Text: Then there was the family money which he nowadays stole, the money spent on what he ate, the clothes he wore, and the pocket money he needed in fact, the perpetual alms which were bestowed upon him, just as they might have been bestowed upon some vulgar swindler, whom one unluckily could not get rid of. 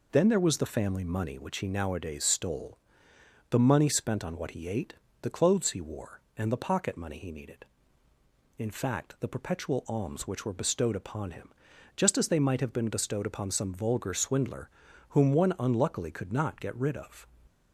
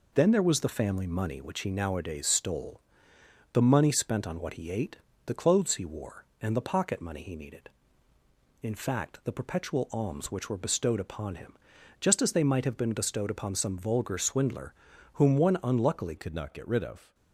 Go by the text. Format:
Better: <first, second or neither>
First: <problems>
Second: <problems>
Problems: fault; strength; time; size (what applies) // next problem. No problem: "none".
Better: first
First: none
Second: changes voice at "could"; from 16.1 s on; 1.0 s long